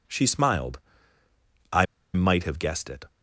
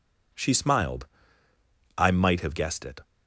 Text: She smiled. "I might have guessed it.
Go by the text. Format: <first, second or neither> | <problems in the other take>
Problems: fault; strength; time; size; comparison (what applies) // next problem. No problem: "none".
second | pauses between "I" and "might"; slight; at 1.8 s; 0.29 s long